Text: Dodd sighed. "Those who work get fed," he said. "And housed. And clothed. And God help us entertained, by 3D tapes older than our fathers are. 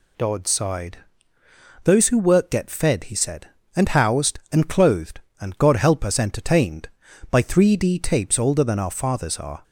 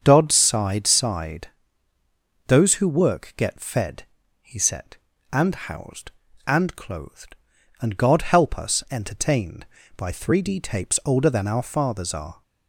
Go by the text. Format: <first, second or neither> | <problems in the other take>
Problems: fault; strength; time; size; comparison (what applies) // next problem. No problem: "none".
first | starts louder than the rest; until 1.0 s; 7 dB // says "sighed" twice; at 0.8 s